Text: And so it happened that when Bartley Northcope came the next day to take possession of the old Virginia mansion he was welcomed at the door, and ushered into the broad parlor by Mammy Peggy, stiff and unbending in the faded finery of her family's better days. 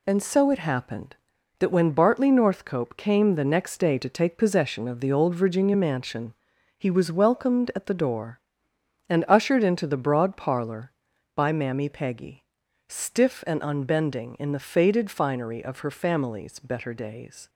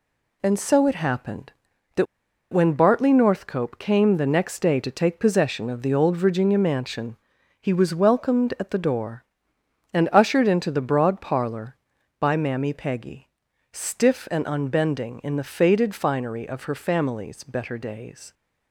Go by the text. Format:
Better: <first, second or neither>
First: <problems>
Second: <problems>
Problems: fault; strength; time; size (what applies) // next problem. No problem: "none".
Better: first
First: pauses between "mansion" and "he"; at 6.3 s; 0.44 s long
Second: pauses between "that" and "when"; noticeable; at 2.0 s; 0.47 s long // pauses between "mansion" and "he"; at 7.1 s; 0.44 s long